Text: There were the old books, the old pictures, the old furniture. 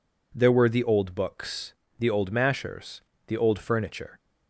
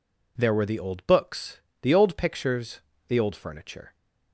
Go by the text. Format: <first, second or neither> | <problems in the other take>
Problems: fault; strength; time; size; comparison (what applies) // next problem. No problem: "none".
second | says "mashers" for "pictures"; at 2.3 s